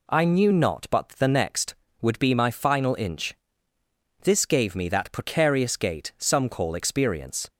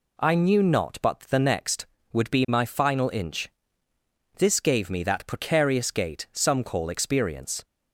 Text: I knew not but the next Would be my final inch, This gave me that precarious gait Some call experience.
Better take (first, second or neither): neither